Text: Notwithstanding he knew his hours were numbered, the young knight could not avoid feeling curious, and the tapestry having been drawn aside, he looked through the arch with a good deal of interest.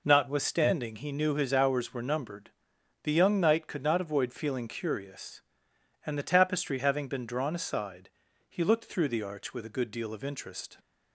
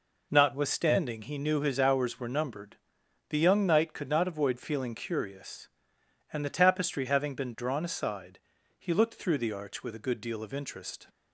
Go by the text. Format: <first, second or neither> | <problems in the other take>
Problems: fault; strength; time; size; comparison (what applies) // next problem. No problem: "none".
neither | none